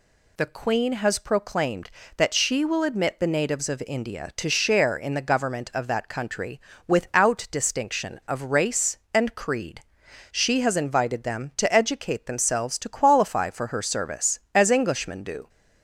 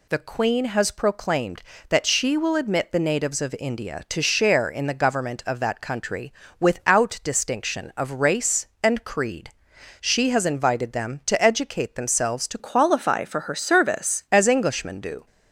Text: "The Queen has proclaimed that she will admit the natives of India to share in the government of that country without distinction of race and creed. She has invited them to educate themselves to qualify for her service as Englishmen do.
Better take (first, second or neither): first